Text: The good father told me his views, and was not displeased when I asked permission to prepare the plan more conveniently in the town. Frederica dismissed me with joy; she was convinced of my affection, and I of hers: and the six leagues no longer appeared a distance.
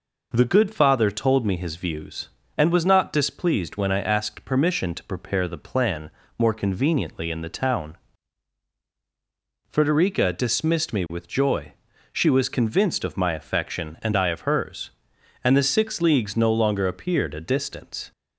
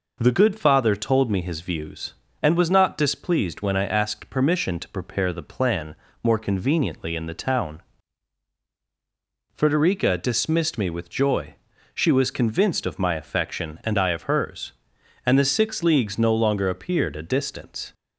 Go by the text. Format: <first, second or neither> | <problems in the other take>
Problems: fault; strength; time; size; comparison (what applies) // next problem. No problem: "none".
neither | pauses between "plan" and "more"; slight; the same in both